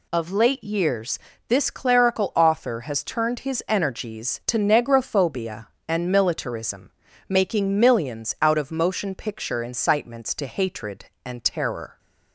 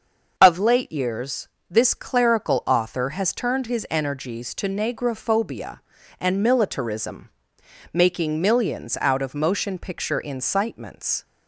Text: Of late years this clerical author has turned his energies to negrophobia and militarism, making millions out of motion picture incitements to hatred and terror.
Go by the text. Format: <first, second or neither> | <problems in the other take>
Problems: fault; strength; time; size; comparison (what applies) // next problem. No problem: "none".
first | starts louder than the rest; until 1.3 s; 6.5 dB // pauses between "years" and "this"; slight; at 1.4 s; 0.22 s long; slight in the first // stops before "to hatred and terror"; at 11.2 s